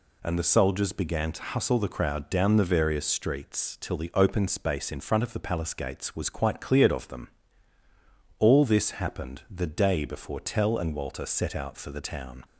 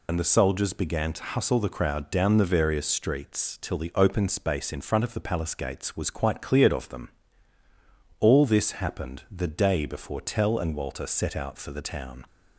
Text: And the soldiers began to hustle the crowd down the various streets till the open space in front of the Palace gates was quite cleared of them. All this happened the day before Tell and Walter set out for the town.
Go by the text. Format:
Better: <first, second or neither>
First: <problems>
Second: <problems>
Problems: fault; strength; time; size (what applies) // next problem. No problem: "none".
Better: first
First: none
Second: loses the start of "And"; at 0.0 s; 65 ms